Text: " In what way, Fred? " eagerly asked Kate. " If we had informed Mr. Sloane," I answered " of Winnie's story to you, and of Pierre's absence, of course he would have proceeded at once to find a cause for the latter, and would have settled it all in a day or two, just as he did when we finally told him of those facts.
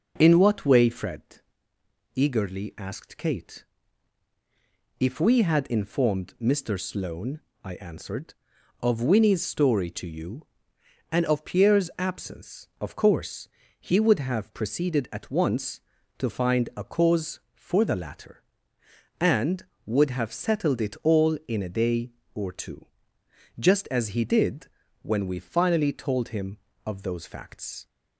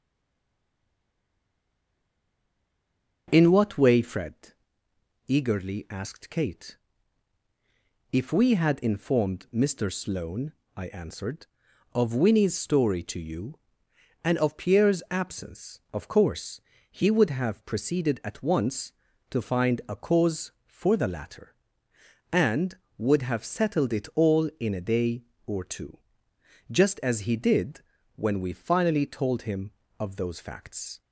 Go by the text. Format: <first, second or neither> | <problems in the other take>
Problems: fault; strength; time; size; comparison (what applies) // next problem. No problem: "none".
first | stays silent before the first word; strong; until 3.2 s; 3.2 s long // starts louder than the rest; until 4.2 s; 7 dB; also in the first // pauses between "course" and "he"; slight; at 16.5 s; 0.30 s long; slight in the first // pauses between "did" and "when"; slight; at 27.8 s; 0.34 s long; slight in the first